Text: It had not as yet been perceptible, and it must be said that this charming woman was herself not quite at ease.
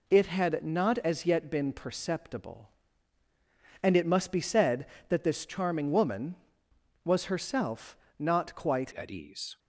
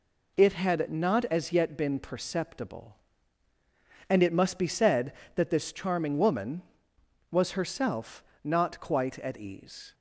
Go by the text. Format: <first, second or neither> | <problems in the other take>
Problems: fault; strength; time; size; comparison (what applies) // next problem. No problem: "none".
second | pauses between "herself" and "not"; slight; at 7.9 s; 0.22 s long; slight in the second // changes voice at "at"; from 8.9 s on; 0.6 s long